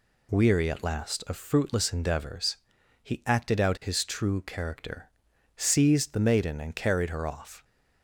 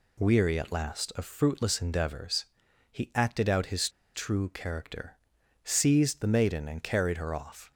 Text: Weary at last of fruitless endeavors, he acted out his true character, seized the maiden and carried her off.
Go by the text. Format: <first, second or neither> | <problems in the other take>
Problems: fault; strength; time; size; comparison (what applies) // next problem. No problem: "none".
first | pauses between "his" and "true"; slight; at 3.8 s; 0.25 s long